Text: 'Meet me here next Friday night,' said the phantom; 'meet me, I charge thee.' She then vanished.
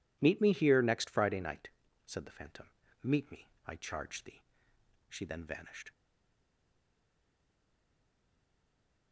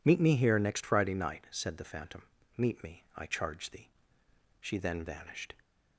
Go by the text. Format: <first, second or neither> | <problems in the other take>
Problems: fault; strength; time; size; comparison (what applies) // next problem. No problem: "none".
second | stays silent after the last word; strong; from 5.9 s on; 3.2 s long